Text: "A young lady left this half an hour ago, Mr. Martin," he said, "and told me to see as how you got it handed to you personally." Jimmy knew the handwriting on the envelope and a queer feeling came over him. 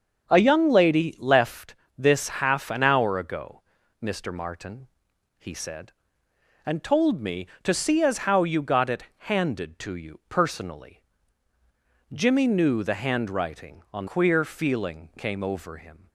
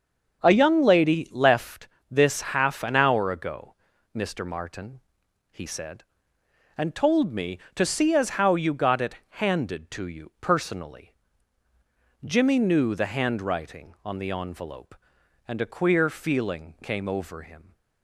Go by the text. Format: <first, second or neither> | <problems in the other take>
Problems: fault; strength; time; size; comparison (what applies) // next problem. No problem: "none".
second | starts louder than the rest; until 1.3 s; 6.5 dB; also in the second // pauses between "left" and "this"; slight; at 1.7 s; 0.20 s long; slight in the second // skips "the envelope and a"; at 14.0 s